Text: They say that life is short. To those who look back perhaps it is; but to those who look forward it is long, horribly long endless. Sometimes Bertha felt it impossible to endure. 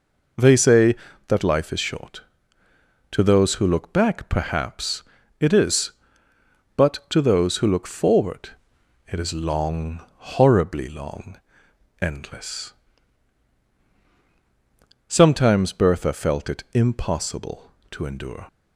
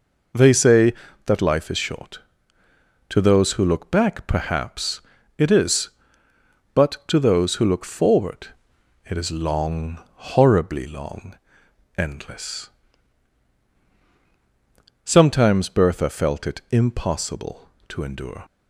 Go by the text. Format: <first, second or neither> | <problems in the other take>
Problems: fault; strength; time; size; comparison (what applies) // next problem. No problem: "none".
neither | pauses between "perhaps" and "it"; slight; the same in both // pauses between "forward" and "it"; noticeable; the same in both // pauses between "long" and "endless"; noticeable; the same in both